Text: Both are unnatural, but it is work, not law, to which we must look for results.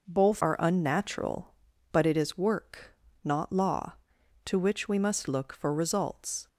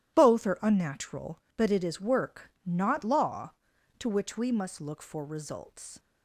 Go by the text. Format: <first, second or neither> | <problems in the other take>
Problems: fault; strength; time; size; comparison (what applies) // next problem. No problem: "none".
second | changes voice at "are"; from 0.4 s on; 6.0 s long